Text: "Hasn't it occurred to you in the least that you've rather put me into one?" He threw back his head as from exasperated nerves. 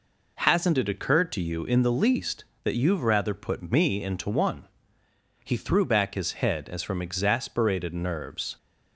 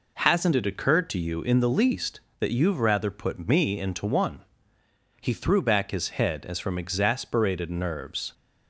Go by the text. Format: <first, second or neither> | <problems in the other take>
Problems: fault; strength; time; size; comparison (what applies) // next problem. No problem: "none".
neither | none